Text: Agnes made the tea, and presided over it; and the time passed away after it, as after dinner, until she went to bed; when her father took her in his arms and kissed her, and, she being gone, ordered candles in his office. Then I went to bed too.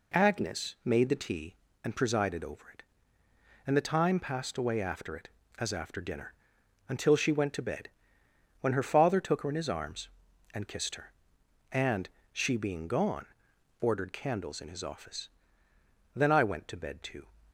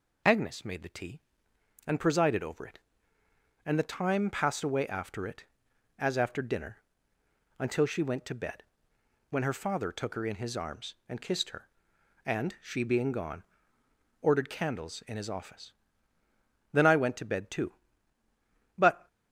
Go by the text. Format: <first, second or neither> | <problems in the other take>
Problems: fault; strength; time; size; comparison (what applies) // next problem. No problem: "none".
first | goes on to say "But"; slight; from 18.7 s on; 0.30 s long